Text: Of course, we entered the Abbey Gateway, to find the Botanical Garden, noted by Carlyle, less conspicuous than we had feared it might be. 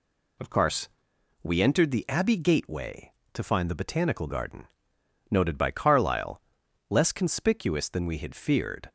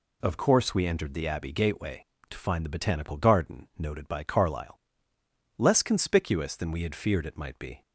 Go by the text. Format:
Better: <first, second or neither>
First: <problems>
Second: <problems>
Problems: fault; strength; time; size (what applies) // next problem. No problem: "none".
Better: second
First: stops before "it might be"; at 8.8 s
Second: none